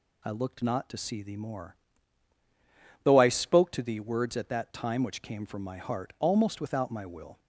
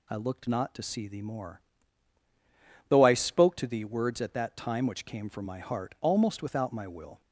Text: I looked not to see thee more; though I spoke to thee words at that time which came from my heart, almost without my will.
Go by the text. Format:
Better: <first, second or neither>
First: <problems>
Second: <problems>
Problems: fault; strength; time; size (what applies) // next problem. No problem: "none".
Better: neither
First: none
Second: none